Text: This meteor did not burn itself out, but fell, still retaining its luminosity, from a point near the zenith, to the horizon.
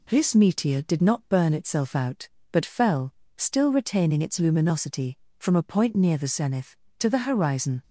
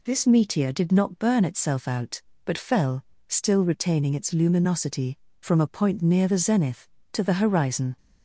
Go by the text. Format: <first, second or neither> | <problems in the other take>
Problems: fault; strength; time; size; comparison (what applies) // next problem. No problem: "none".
neither | none